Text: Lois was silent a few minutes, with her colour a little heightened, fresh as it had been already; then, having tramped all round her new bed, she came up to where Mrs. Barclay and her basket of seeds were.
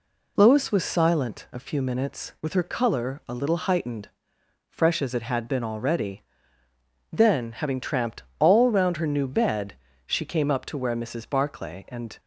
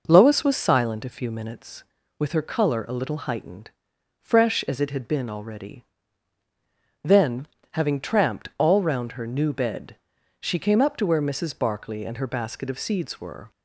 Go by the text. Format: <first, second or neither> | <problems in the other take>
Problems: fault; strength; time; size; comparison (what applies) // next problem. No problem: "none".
second | pauses between "tramped" and "all"; slight; at 8.2 s; 0.16 s long // stops before "her basket of seeds were"; at 12.1 s